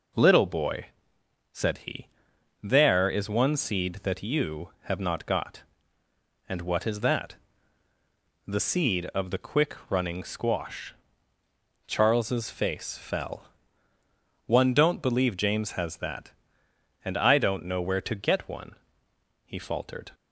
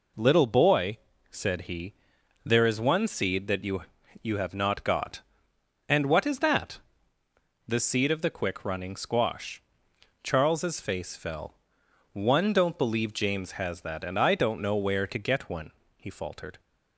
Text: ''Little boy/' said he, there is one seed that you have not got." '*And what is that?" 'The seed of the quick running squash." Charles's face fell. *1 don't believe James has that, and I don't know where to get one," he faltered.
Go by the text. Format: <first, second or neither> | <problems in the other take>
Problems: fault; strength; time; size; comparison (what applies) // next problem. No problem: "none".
first | says "you" twice; at 4.2 s